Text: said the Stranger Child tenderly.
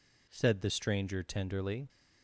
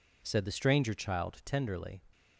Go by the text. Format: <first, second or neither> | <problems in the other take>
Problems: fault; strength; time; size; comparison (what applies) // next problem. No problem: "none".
second | skips "Child"; at 1.2 s